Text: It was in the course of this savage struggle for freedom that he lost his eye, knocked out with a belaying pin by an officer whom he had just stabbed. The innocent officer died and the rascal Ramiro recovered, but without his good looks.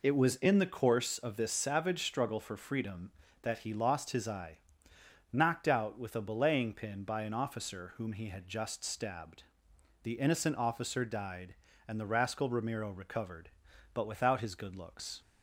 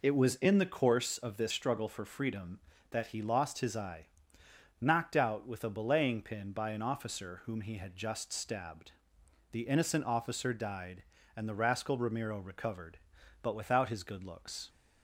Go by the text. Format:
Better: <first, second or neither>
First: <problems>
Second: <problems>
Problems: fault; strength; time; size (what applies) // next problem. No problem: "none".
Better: first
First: none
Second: skips "savage"; at 1.5 s